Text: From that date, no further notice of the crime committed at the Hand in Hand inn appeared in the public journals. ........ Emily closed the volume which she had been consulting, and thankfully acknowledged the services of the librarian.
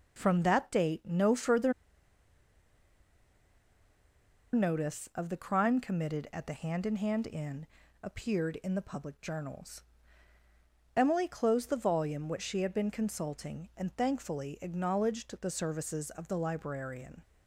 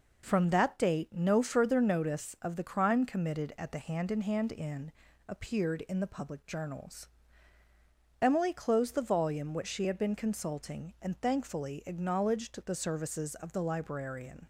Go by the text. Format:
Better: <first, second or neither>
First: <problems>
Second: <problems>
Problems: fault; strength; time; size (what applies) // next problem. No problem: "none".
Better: second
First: pauses between "further" and "notice"; strong; at 1.7 s; 2.8 s long // pauses between "inn" and "appeared"; slight; at 7.6 s; 0.34 s long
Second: pauses between "inn" and "appeared"; slight; at 4.9 s; 0.34 s long